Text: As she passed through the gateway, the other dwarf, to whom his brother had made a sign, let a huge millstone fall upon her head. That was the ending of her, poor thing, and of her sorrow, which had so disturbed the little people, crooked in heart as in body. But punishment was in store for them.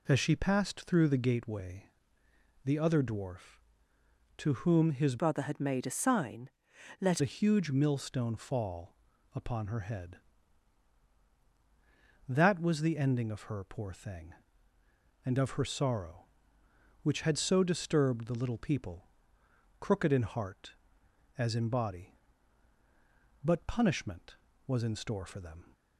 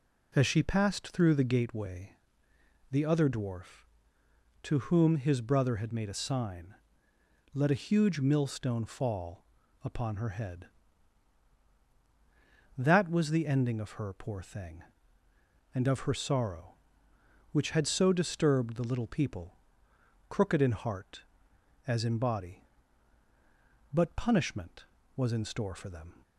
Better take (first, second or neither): second